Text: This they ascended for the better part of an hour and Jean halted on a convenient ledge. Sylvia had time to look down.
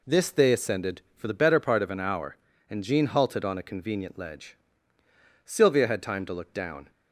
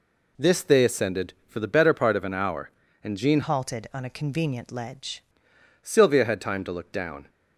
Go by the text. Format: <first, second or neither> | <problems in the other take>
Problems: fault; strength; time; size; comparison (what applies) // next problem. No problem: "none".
first | changes voice from "halted" to "ledge"; from 3.4 to 5.2 s; 1.8 s long